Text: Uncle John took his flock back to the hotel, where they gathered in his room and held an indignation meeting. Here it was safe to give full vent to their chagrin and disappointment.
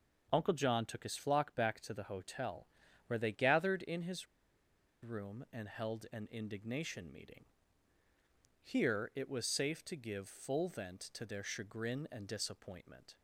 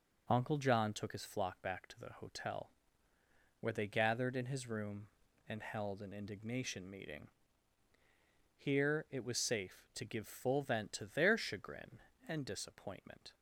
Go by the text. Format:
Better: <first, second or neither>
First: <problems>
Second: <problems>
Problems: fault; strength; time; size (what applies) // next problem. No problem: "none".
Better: second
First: pauses between "his" and "room"; noticeable; at 4.2 s; 0.77 s long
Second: none